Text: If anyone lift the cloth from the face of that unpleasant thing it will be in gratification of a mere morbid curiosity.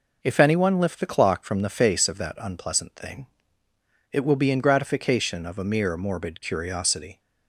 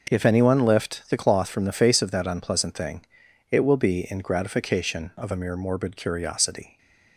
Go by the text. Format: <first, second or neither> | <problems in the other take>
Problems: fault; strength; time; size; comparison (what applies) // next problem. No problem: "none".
second | says "clock" for "cloth"; at 1.0 s // pauses between "thing" and "it"; noticeable; at 3.2 s; 0.84 s long; noticeable in the second